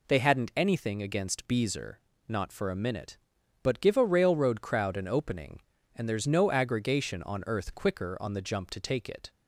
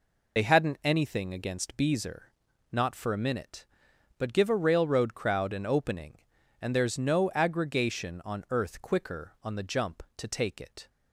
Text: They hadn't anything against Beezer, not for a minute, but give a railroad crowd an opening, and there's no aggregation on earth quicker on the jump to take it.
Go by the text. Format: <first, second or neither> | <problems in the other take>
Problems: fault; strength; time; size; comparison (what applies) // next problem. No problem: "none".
first | loses the start of "They"; at 0.3 s; 50 ms